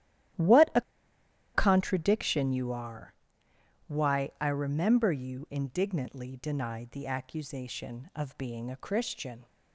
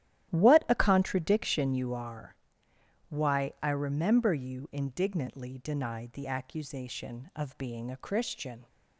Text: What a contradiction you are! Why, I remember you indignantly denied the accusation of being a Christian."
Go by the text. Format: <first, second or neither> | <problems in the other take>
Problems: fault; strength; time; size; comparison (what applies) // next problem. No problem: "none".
second | starts louder than the rest; strong; until 2.1 s; 12.5 dB; strong in the second // pauses between "a" and "contradiction"; noticeable; at 0.8 s; 0.74 s long